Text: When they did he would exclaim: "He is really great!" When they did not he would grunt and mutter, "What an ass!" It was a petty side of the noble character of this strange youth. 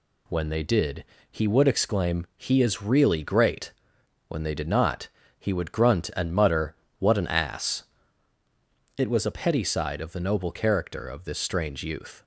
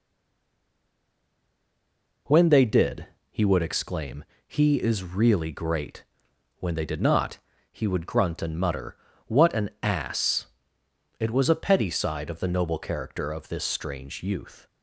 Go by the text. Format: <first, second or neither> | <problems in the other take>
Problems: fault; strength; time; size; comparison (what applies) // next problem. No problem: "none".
first | stays silent before the first word; until 2.2 s; 2.2 s long // pauses between "did" and "he"; slight; at 3.0 s; 0.24 s long; slight in the first // pauses between "not" and "he"; slight; at 7.3 s; 0.34 s long; slight in the first